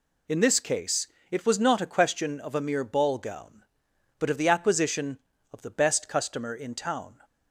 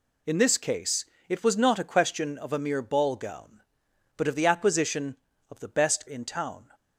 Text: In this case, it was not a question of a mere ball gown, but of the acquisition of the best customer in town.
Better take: first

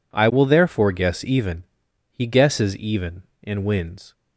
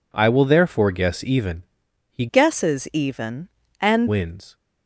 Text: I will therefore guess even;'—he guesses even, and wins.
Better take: first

